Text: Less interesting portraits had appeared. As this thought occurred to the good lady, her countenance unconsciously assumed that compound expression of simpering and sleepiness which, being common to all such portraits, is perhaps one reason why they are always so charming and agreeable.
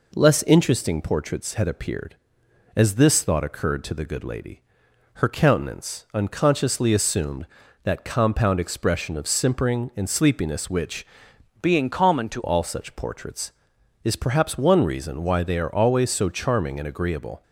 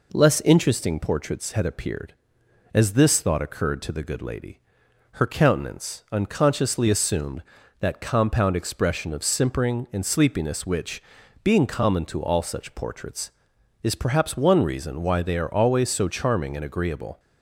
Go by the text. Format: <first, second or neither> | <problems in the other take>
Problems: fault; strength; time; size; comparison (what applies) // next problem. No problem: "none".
second | changes voice from "being" to "to"; from 11.6 to 12.4 s; 0.8 s long